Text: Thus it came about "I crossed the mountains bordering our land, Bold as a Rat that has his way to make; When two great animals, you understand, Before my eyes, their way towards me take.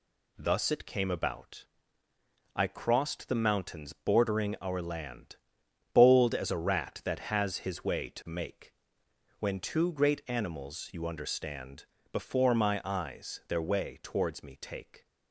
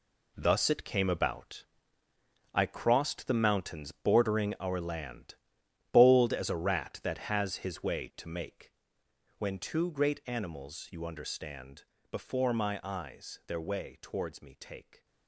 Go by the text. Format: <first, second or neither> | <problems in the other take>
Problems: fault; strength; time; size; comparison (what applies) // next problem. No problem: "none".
first | gets quieter; strong; throughout; 9.5 dB // pauses between "about" and "I"; noticeable; at 1.6 s; 0.88 s long; noticeable in the first